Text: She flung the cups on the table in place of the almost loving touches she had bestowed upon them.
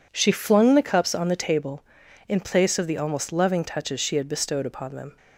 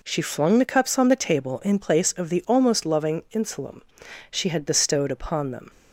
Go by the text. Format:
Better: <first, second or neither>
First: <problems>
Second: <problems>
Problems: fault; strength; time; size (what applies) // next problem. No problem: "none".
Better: first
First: none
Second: says "insulum" for "touches"; at 3.3 s